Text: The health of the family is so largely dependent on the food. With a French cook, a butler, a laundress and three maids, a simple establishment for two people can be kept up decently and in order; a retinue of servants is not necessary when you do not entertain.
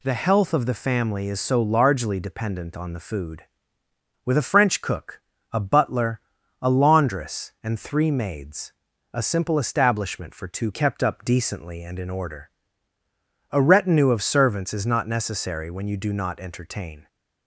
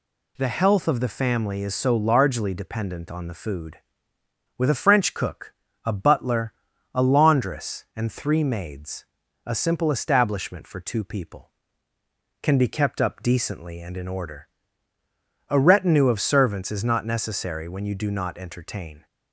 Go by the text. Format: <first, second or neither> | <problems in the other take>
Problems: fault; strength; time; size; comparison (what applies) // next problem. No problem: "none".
second | skips "people can be"; at 10.7 s